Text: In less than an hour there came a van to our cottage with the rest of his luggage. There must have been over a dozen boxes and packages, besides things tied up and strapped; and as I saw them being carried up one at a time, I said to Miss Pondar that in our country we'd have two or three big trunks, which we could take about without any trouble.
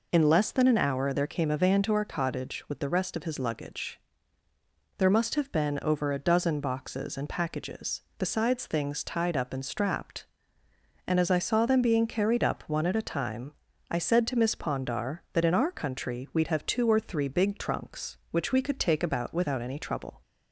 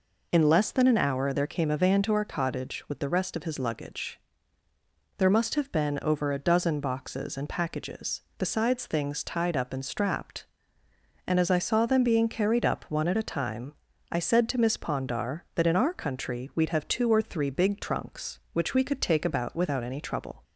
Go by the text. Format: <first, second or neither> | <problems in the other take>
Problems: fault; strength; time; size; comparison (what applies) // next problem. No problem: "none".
neither | none